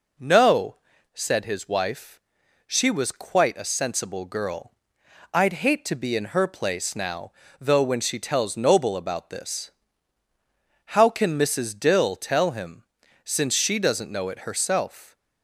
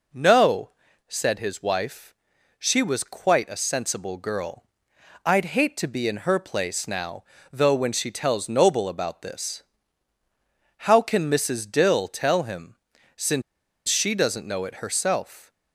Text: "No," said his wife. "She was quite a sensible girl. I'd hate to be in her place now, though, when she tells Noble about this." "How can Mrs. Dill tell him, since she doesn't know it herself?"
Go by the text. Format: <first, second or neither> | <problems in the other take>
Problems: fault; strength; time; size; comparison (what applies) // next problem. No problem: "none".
first | pauses between "since" and "she"; noticeable; at 13.4 s; 0.46 s long